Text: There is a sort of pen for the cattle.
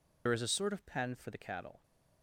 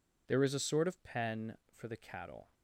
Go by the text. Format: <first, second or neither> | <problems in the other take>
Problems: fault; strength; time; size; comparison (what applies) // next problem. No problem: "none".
second | loses the start of "There"; at 0.2 s; 70 ms